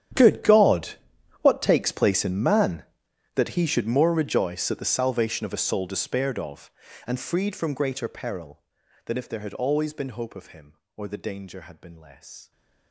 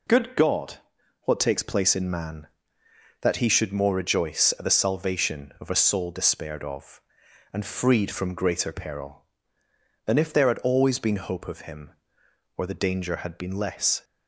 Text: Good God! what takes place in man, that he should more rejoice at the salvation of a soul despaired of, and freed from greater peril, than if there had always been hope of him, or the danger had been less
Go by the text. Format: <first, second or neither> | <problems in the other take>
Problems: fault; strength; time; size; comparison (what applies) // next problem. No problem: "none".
second | gets quieter; strong; throughout; 20.5 dB